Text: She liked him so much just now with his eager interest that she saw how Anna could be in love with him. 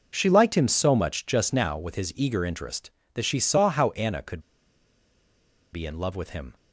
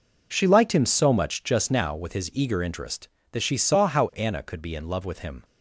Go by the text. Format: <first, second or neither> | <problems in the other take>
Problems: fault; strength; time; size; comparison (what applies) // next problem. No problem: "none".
second | pauses between "could" and "be"; strong; at 4.4 s; 1.3 s long